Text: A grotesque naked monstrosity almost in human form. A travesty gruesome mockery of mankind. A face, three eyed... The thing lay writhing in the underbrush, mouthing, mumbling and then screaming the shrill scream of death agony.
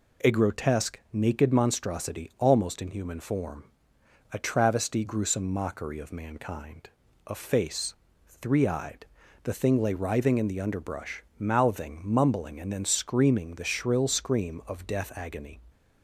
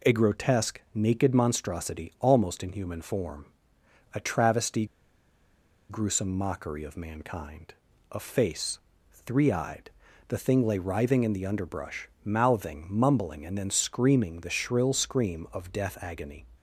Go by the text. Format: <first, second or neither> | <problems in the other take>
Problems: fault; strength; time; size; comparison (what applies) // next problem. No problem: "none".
first | pauses between "travesty" and "gruesome"; at 4.8 s; 1.0 s long